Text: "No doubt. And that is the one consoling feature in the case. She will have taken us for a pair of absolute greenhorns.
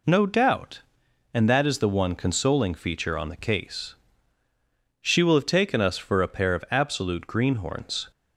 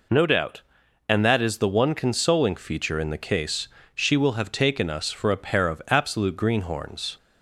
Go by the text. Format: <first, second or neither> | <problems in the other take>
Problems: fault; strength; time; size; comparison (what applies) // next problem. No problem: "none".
second | says "on" for "in"; at 3.1 s